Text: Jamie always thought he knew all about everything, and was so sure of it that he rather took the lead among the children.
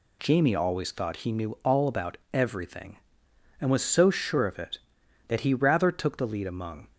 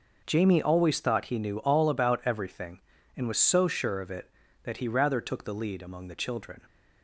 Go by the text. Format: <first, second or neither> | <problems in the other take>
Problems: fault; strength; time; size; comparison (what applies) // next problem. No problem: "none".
second | pauses between "about" and "everything"; slight; at 2.1 s; 0.16 s long // stops before "the children"; at 6.9 s